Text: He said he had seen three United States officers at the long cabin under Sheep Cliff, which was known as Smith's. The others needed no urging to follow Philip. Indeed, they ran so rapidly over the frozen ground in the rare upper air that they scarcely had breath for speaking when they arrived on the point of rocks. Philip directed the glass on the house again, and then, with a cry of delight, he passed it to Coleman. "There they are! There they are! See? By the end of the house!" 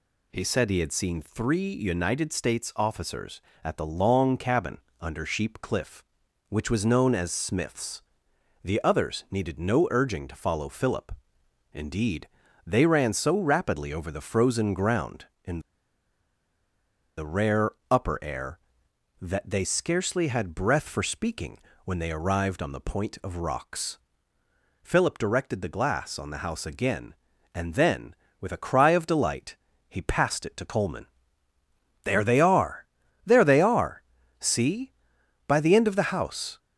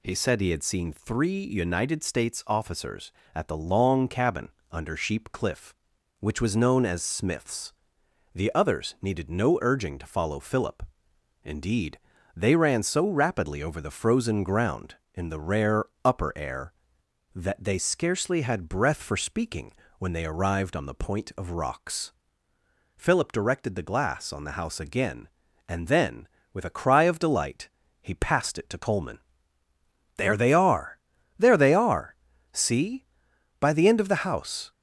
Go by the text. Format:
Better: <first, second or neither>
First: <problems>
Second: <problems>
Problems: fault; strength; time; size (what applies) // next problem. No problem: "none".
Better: second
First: pauses between "cabin" and "under"; slight; at 4.7 s; 0.22 s long // pauses between "in" and "the"; strong; at 15.6 s; 1.5 s long // pauses between "rare" and "upper"; slight; at 17.7 s; 0.18 s long // pauses between "speaking" and "when"; slight; at 21.5 s; 0.26 s long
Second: pauses between "cabin" and "under"; slight; at 4.4 s; 0.22 s long // pauses between "rare" and "upper"; slight; at 15.8 s; 0.18 s long // pauses between "speaking" and "when"; slight; at 19.7 s; 0.26 s long